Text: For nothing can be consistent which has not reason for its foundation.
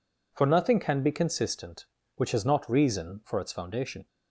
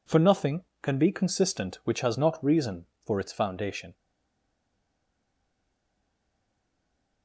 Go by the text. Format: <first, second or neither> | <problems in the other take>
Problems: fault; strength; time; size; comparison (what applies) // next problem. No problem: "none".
first | stays silent after the last word; strong; from 3.9 s on; 3.3 s long